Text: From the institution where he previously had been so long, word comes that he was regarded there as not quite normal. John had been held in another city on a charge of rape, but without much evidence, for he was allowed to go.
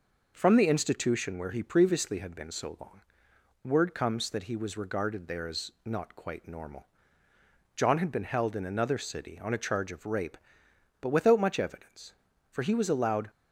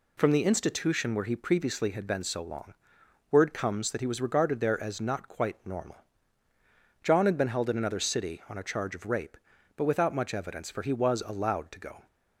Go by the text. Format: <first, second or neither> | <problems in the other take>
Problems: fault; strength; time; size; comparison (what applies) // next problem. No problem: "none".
second | pauses between "as" and "not"; slight; at 5.6 s; 0.16 s long // stops before "to go"; at 13.2 s